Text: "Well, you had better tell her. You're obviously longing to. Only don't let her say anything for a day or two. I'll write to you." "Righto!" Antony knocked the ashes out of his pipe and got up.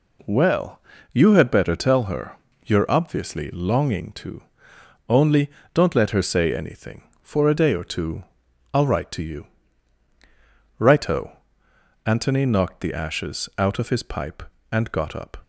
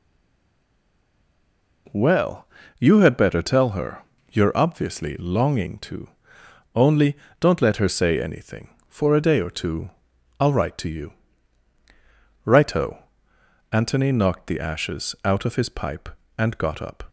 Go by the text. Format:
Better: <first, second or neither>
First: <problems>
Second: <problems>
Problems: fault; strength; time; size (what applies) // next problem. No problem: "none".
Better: first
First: pauses between "Only" and "don't"; slight; at 5.4 s; 0.24 s long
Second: stays silent before the first word; noticeable; until 1.8 s; 1.8 s long // pauses between "Only" and "don't"; slight; at 7.1 s; 0.24 s long